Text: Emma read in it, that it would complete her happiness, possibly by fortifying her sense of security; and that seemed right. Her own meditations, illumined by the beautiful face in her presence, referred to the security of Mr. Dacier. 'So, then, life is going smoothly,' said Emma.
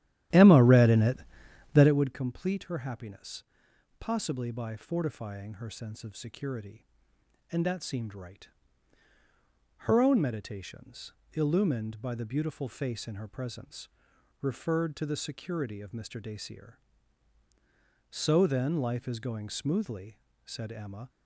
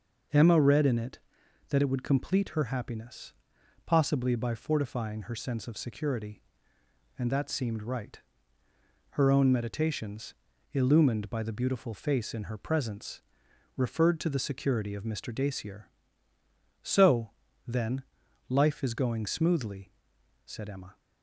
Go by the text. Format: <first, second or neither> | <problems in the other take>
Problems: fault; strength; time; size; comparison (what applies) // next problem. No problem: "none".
second | starts louder than the rest; strong; until 2.1 s; 12.5 dB